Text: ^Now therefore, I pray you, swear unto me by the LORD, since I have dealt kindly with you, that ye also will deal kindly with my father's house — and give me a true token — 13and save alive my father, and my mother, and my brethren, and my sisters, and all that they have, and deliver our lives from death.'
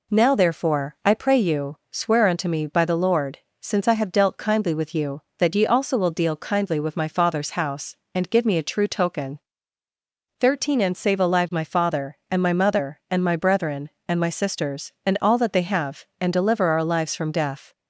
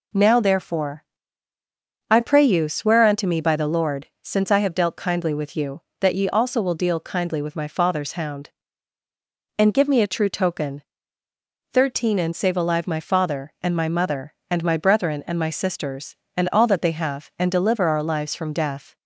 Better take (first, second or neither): first